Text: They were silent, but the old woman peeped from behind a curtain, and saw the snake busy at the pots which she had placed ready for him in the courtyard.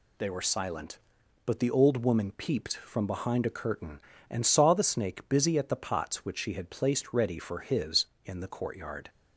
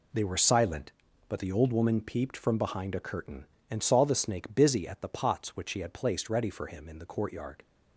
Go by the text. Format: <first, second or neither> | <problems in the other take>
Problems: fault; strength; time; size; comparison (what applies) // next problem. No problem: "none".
second | says "his" for "him"; at 7.6 s